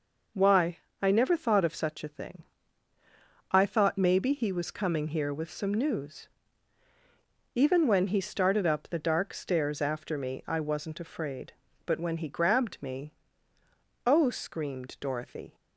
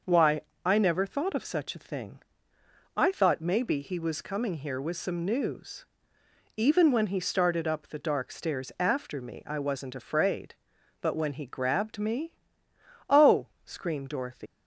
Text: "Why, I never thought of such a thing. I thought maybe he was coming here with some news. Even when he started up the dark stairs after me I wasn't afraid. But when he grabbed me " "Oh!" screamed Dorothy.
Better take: first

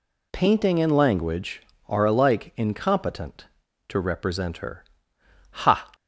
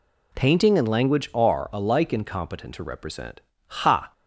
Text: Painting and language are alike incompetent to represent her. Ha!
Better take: first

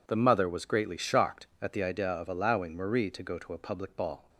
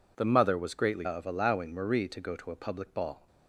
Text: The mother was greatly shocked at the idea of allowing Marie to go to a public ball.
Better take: first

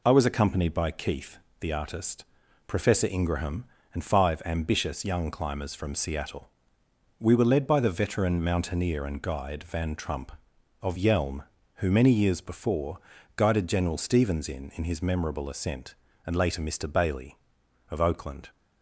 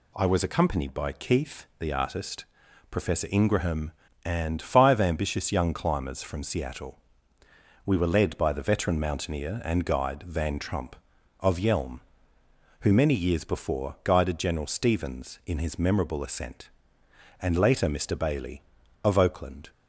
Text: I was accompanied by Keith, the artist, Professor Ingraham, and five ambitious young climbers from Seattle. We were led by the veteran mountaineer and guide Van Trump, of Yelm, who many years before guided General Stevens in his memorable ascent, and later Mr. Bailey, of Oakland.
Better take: second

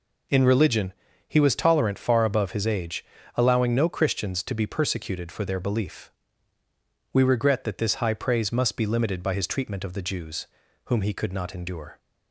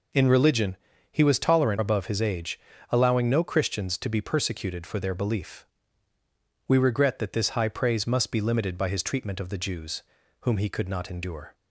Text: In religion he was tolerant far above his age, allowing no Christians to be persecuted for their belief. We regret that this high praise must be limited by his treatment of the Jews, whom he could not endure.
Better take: first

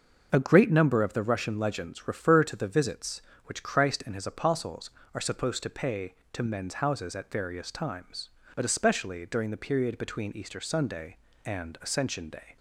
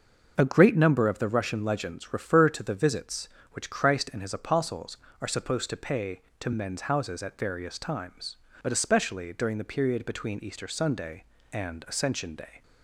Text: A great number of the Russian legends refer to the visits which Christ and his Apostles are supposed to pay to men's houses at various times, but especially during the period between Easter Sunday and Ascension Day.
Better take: neither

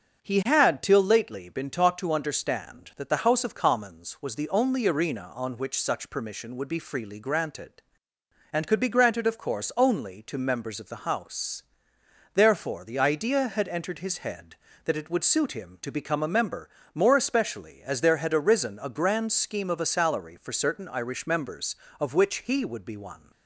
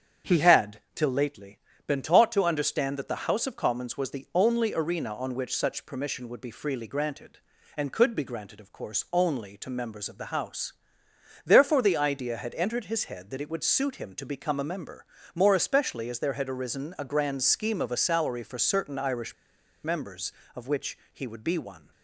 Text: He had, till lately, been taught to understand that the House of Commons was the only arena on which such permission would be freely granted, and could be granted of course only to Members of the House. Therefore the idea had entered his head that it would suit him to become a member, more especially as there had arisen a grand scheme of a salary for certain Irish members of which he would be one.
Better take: first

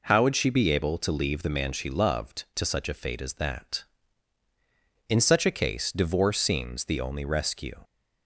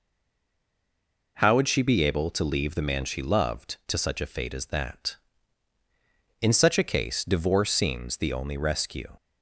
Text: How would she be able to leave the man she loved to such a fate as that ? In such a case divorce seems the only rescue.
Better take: first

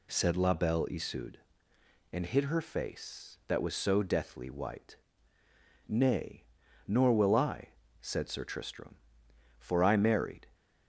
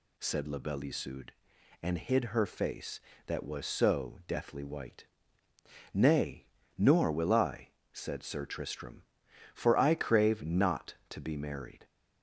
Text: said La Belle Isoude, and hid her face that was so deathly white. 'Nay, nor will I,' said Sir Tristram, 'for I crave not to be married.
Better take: second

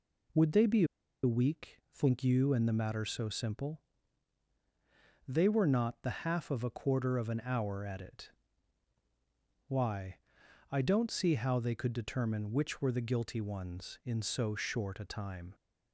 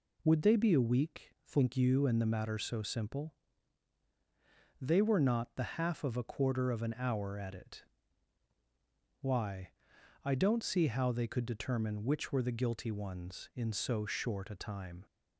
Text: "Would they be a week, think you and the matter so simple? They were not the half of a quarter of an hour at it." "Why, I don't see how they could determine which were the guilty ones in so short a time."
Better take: second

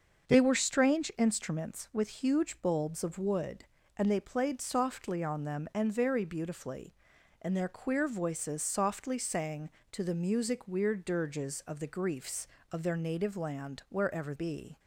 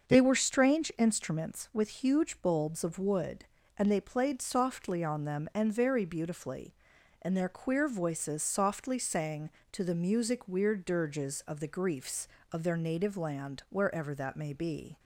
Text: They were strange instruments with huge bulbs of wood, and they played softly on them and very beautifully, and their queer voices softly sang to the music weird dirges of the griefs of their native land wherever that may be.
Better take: second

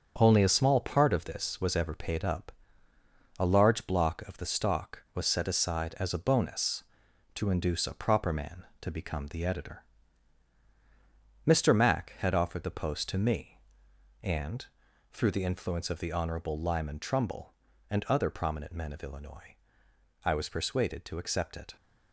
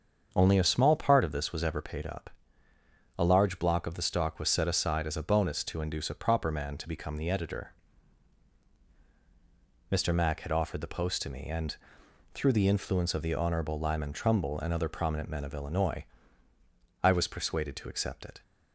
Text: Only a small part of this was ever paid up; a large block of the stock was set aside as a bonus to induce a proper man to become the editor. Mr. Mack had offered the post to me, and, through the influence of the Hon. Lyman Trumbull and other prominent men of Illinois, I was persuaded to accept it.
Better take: second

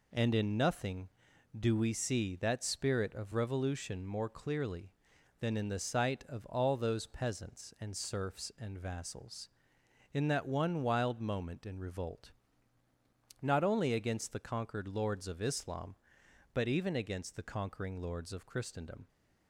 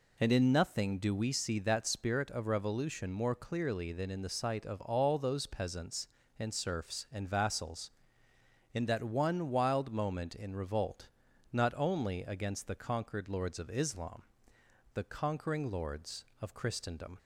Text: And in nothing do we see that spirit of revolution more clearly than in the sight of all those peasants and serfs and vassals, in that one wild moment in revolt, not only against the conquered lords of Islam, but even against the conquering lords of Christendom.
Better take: first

